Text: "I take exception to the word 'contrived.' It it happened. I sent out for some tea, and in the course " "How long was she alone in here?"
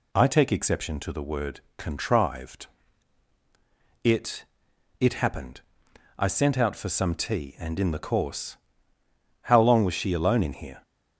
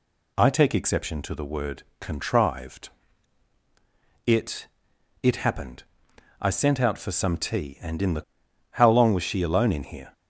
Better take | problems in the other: first | pauses between "word" and "contrived"; slight; at 1.8 s; 0.16 s long; slight in the first // pauses between "It" and "it"; noticeable; at 4.6 s; 0.56 s long; noticeable in the first // skips "course"; at 8.2 s

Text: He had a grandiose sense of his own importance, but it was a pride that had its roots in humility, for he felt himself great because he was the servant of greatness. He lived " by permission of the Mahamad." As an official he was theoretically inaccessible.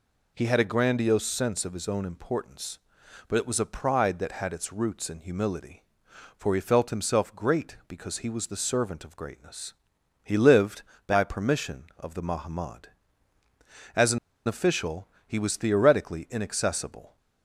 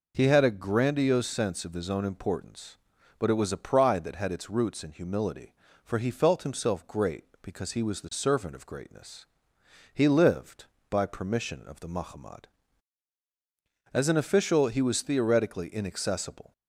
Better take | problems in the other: second | pauses between "an" and "official"; slight; at 14.1 s; 0.28 s long // pauses between "official" and "he"; slight; at 15.0 s; 0.18 s long

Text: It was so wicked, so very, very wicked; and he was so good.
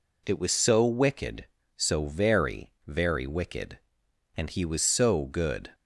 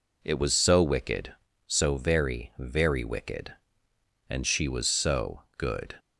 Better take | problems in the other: first | says "she" for "he"; at 4.4 s // pauses between "so" and "good"; slight; at 5.4 s; 0.16 s long

